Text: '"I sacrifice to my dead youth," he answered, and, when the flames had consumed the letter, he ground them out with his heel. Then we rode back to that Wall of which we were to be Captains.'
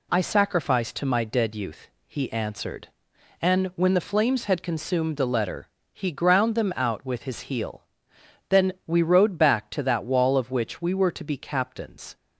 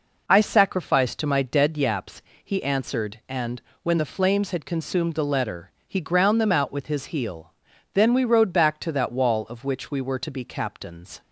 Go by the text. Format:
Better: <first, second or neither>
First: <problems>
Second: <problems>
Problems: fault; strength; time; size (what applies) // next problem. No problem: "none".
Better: first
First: none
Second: says "yaps" for "youth"; at 1.7 s